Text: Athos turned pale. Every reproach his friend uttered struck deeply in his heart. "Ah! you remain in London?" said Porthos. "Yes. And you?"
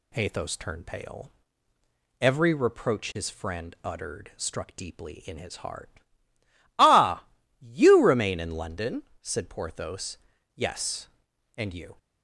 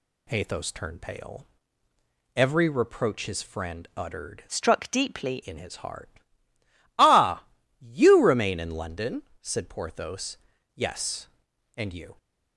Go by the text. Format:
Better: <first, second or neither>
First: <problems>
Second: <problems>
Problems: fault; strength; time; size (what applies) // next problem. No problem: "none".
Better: first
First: none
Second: changes voice from "struck" to "deeply"; from 4.4 to 5.4 s; 1.0 s long